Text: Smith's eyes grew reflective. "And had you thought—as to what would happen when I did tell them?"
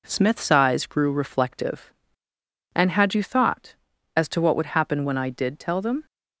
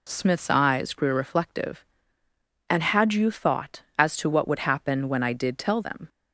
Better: neither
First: none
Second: none

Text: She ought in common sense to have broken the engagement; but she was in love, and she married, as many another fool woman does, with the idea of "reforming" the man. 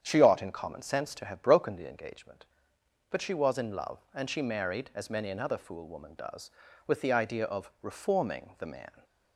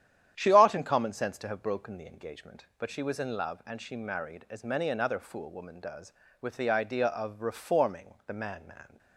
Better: first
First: starts louder than the rest; strong; until 1.0 s; 8 dB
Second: starts louder than the rest; strong; until 1.3 s; 10 dB // says "man" twice; at 8.6 s

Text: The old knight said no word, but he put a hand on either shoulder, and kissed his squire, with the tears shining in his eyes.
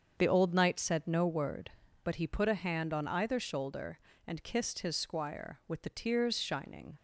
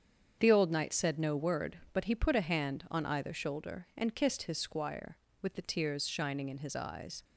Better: second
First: starts louder than the rest; until 1.1 s; 7 dB // stops before "in his eyes"; at 6.9 s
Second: starts louder than the rest; strong; until 1.4 s; 7.5 dB

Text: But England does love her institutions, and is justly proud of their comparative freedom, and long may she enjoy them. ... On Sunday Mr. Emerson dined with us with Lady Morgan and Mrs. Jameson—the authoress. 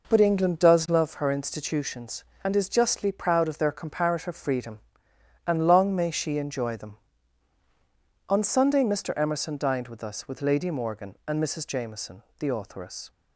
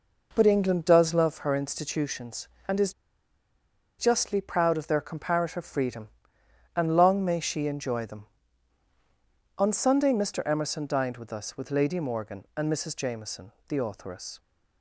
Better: first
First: none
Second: pauses between "is" and "justly"; at 2.9 s; 1.0 s long

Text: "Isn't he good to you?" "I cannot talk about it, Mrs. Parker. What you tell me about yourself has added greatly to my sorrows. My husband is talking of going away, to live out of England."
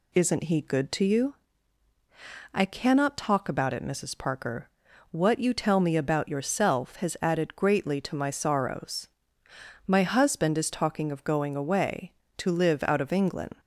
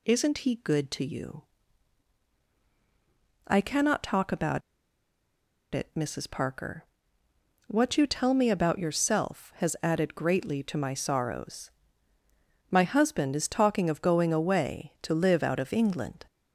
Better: first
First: none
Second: pauses between "about" and "it"; at 4.6 s; 1.1 s long

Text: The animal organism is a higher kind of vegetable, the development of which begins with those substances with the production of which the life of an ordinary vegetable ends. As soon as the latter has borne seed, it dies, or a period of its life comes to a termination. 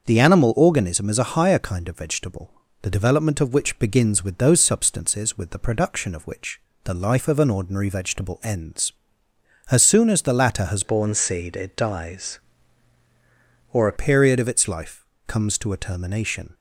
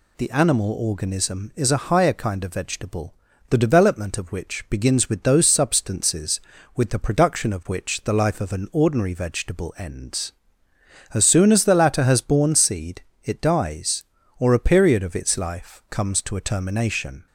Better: second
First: starts louder than the rest; noticeable; until 1.1 s; 6 dB // pauses between "which" and "the"; slight; at 6.5 s; 0.26 s long // changes voice from "borne" to "a"; from 10.8 to 13.9 s; 3.1 s long // pauses between "life" and "comes"; slight; at 15.0 s; 0.20 s long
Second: none

